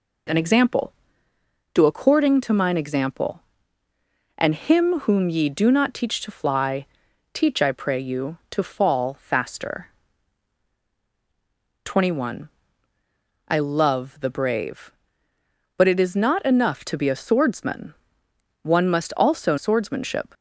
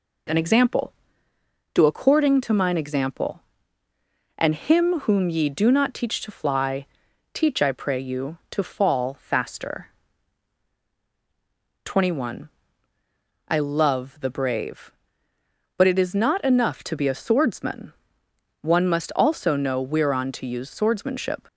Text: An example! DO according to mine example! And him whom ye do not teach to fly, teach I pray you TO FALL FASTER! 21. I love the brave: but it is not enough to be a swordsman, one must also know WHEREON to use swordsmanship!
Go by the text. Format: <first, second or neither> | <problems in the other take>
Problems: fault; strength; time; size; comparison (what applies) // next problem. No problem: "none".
second | skips "know WHEREON to use"; at 19.5 s